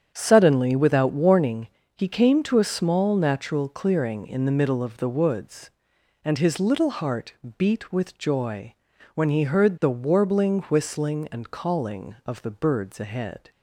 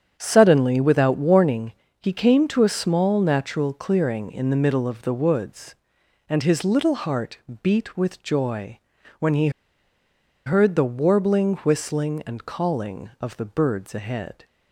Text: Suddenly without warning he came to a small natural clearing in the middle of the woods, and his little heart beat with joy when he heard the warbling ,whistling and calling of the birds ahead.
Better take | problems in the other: first | starts louder than the rest; strong; until 1.2 s; 8 dB; strong in the first // pauses between "warning" and "he"; slight; at 1.7 s; 0.28 s long; slight in the first // pauses between "heart" and "beat"; slight; at 7.3 s; 0.22 s long; slight in the first // pauses between "joy" and "when"; at 8.7 s; 0.40 s long; also in the first // pauses between "he" and "heard"; noticeable; at 9.4 s; 0.96 s long

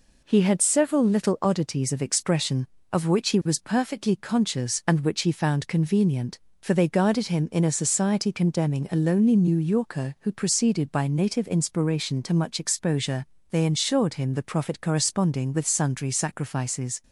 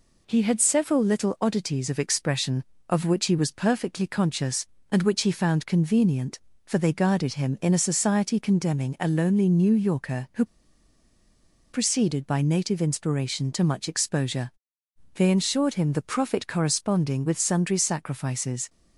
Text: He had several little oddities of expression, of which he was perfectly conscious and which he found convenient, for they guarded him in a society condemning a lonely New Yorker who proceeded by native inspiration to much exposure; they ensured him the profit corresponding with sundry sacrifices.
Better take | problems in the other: first | pauses between "who" and "proceeded"; strong; at 10.4 s; 1.2 s long

